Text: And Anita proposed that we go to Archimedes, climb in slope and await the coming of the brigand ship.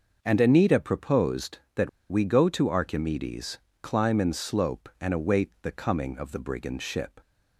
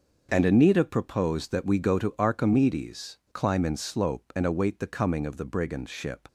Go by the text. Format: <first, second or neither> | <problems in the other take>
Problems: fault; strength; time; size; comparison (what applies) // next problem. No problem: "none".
second | starts louder than the rest; noticeable; until 1.2 s; 6 dB; also in the second // pauses between "that" and "we"; slight; at 1.8 s; 0.20 s long